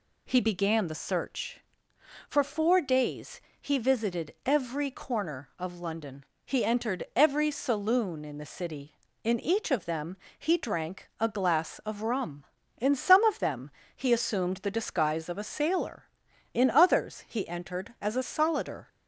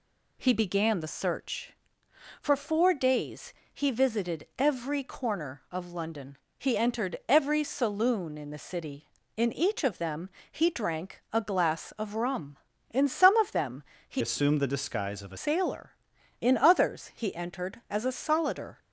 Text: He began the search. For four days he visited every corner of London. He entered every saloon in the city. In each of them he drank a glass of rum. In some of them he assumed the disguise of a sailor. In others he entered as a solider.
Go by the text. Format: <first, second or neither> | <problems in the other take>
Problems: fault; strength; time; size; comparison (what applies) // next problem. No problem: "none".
first | pauses between "days" and "he"; slight; at 3.5 s; 0.22 s long; slight in the first // pauses between "them" and "he"; slight; at 10.2 s; 0.20 s long; slight in the first // pauses between "them" and "he"; slight; at 13.8 s; 0.26 s long; slight in the first // changes voice from "assumed" to "a"; from 14.2 to 15.3 s; 1.1 s long